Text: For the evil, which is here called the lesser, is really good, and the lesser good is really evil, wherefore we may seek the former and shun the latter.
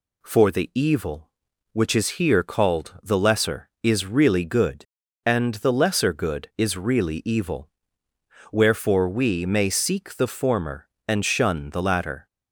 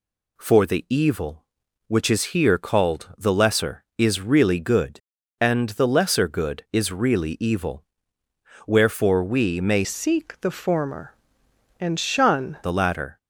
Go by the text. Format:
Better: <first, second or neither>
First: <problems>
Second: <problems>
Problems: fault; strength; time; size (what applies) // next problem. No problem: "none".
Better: first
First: none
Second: changes voice from "seek" to "shun"; from 9.8 to 12.5 s; 2.7 s long